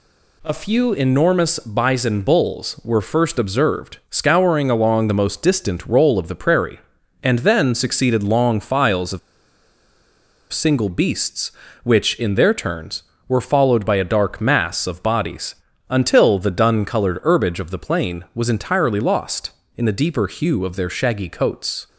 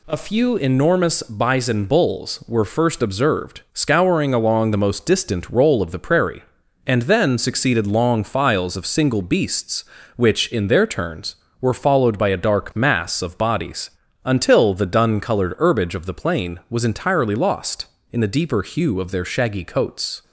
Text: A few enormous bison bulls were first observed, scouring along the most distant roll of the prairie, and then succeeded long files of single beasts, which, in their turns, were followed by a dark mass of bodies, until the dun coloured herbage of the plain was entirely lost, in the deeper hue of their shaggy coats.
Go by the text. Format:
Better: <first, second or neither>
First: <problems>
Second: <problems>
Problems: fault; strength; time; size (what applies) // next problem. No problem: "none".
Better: second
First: pauses between "of" and "single"; strong; at 9.1 s; 1.3 s long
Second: none